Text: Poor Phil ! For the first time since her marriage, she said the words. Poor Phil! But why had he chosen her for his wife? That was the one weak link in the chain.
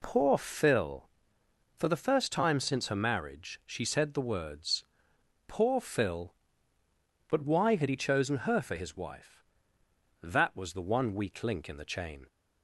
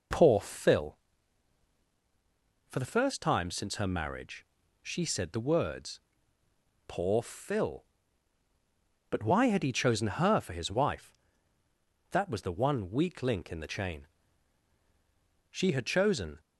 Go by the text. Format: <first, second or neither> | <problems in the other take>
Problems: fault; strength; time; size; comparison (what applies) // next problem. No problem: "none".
first | goes on to say "She had chosen"; noticeable; from 15.5 s on; 0.88 s long